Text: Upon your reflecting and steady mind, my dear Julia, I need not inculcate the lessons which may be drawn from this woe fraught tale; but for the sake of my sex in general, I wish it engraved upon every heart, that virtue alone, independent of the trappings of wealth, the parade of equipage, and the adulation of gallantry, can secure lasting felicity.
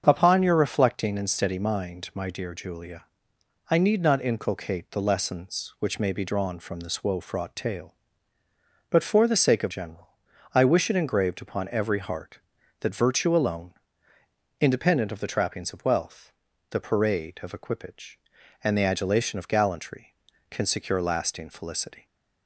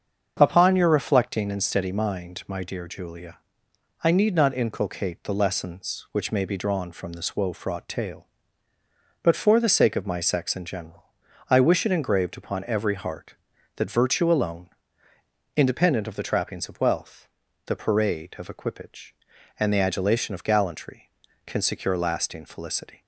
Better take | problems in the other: second | starts louder than the rest; until 1.0 s; 7 dB; also in the second // skips "my sex in"; at 9.7 s

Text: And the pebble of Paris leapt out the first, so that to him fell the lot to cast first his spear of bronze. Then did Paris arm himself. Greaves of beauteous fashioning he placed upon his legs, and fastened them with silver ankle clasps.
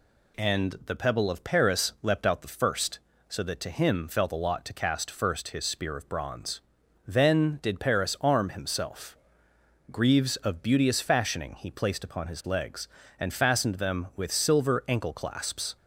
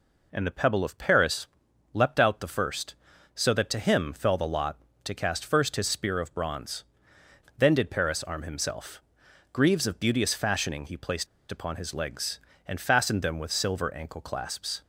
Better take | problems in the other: first | pauses between "Paris" and "leapt"; noticeable; at 1.4 s; 0.48 s long // pauses between "placed" and "upon"; slight; at 11.2 s; 0.25 s long

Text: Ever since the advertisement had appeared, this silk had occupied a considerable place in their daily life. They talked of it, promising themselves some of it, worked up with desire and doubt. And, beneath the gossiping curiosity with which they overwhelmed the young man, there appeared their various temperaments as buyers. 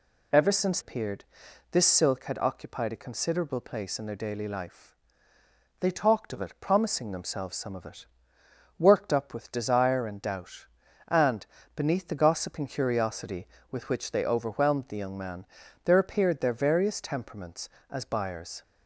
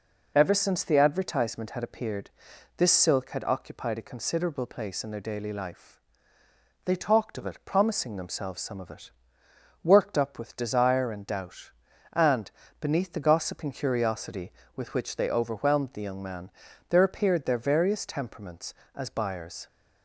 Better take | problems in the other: second | skips "the advertisement had"; at 0.7 s

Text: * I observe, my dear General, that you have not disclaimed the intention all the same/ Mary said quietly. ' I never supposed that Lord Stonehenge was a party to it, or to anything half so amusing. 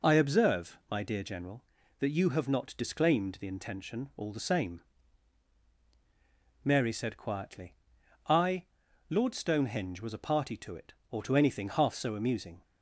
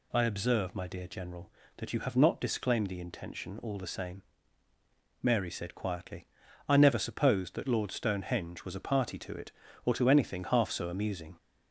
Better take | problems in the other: second | skips "never supposed that"; at 8.8 s

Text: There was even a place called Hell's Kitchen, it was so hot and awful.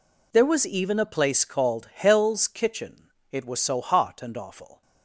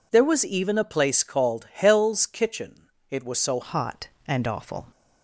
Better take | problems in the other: first | changes voice at "hot"; from 3.6 s on; 1.2 s long

